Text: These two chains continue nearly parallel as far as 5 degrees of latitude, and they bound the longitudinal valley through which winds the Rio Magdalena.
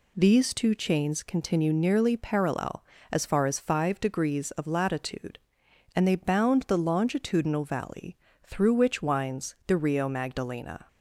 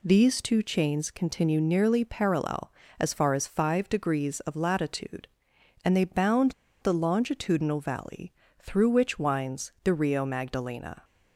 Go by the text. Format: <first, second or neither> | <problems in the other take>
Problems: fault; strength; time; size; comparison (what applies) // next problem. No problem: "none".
first | pauses between "bound" and "the"; slight; at 6.5 s; 0.29 s long // pauses between "valley" and "through"; slight; at 8.3 s; 0.26 s long; slight in the first